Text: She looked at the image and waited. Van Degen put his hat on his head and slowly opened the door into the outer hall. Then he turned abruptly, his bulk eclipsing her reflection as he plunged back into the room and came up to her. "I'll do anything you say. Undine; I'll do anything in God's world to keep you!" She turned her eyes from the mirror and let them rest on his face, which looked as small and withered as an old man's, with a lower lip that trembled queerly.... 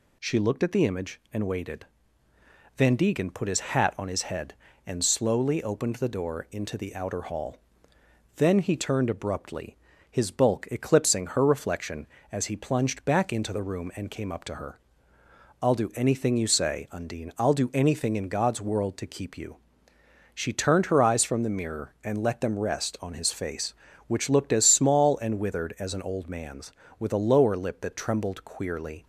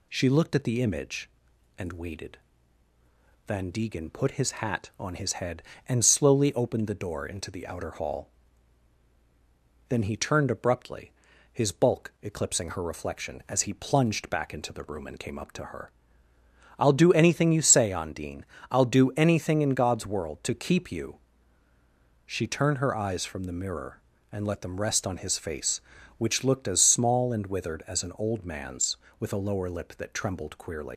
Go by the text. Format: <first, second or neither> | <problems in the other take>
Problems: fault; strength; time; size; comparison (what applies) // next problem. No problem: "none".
first | leaves "queerly" unfinished; at 30.9 s; 80 ms